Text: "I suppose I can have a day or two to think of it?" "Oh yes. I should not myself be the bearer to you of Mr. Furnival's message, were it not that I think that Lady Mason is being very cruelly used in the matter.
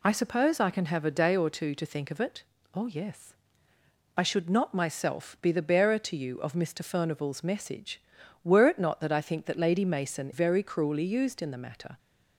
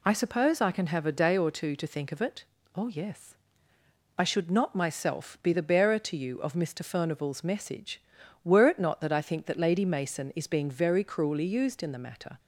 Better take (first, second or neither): second